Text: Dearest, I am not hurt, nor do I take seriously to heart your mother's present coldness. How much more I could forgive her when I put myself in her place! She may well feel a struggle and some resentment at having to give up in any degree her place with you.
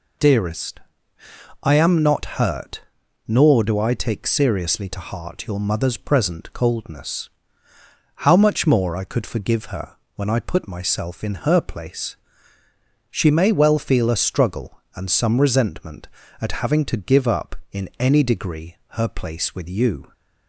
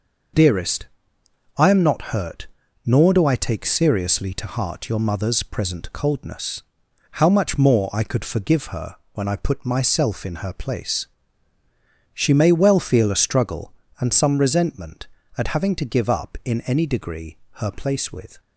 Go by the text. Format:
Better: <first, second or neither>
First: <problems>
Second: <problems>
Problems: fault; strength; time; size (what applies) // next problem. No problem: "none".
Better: first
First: pauses between "her" and "when"; slight; at 9.9 s; 0.18 s long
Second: pauses between "her" and "when"; slight; at 8.9 s; 0.16 s long // pauses between "degree" and "her"; slight; at 17.3 s; 0.22 s long // stops before "you"; at 18.3 s